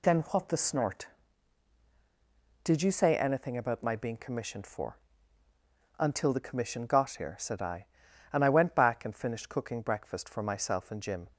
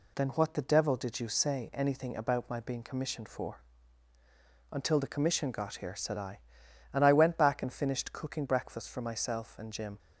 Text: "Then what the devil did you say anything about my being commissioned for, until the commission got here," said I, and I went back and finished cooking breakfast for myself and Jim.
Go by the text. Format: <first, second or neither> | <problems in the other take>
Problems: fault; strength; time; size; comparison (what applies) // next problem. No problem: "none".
second | says "snort" for "devil"; at 0.5 s